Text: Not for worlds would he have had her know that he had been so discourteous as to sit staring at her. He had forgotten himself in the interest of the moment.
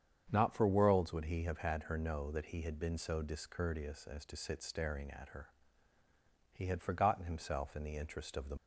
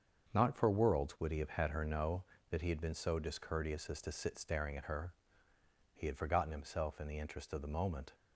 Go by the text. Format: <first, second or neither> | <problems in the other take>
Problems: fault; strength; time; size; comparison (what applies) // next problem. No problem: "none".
second | starts louder than the rest; strong; until 1.3 s; 8 dB; also in the second // stops before "moment"; at 8.5 s